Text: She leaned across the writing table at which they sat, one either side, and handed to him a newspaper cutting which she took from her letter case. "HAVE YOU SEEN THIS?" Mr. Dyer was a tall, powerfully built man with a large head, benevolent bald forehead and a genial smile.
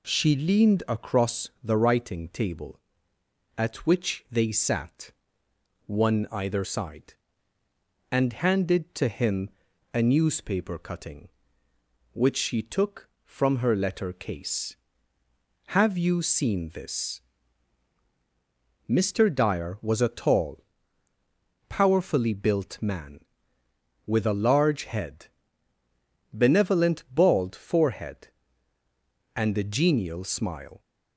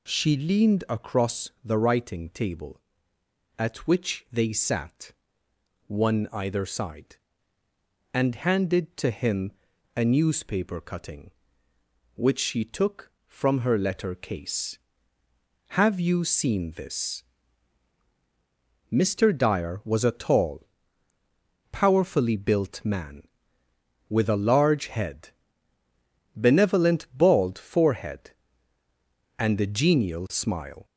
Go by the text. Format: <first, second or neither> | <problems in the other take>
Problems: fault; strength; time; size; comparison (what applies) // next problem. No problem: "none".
first | gets louder; throughout; 3.5 dB // pauses between "him" and "a"; noticeable; at 9.5 s; 0.46 s long; noticeable in the first